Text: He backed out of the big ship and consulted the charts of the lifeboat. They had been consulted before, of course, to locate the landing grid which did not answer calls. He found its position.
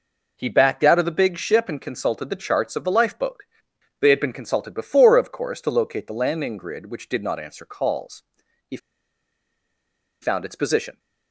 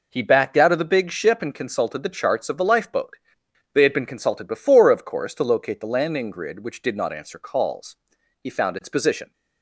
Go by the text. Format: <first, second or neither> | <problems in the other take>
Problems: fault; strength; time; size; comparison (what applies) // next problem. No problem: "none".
second | pauses between "He" and "found"; strong; at 8.7 s; 1.4 s long